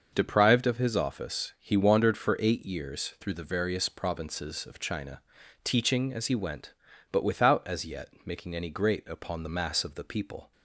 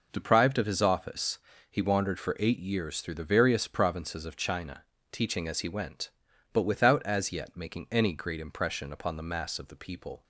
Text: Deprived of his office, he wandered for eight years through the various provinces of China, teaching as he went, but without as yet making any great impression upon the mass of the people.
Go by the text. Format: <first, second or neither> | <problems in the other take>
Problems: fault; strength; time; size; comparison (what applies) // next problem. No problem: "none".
second | starts louder than the rest; noticeable; until 1.1 s; 6 dB // skips "impression"; at 9.0 s